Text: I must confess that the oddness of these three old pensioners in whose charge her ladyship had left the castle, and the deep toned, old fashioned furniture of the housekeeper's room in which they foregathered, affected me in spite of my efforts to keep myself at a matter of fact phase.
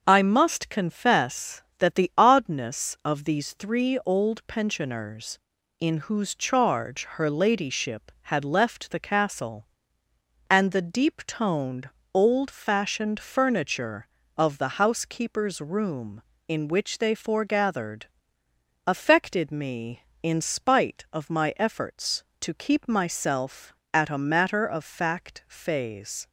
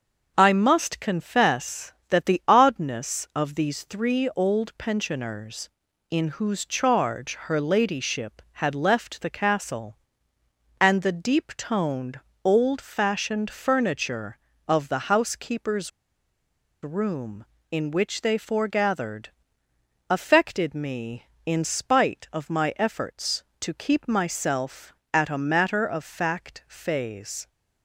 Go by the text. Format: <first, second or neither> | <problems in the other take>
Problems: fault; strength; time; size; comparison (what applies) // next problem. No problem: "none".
first | starts louder than the rest; until 1.3 s; 6.5 dB; also in the first // pauses between "housekeeper's" and "room"; noticeable; at 15.9 s; 0.94 s long